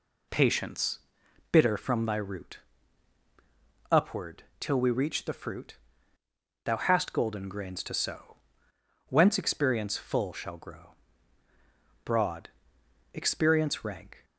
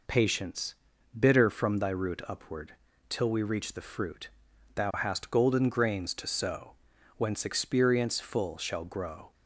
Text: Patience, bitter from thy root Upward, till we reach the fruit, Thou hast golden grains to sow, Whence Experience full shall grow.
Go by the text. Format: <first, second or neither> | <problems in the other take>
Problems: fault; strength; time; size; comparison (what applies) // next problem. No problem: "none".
second | pauses between "root" and "Upward"; strong; at 2.5 s; 1.3 s long // goes on to say "Broad Experience rank"; strong; from 12.0 s on; 2.2 s long